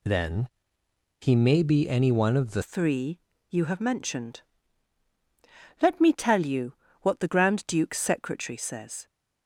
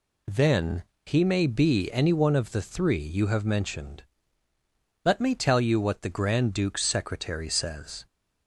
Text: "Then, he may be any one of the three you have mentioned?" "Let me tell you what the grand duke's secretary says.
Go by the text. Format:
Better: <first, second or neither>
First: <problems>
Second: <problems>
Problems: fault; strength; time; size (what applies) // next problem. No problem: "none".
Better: second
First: changes voice at "three"; from 2.6 s on; 6.4 s long // pauses between "three" and "you"; slight; at 3.1 s; 0.32 s long // pauses between "you" and "what"; slight; at 6.7 s; 0.30 s long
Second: none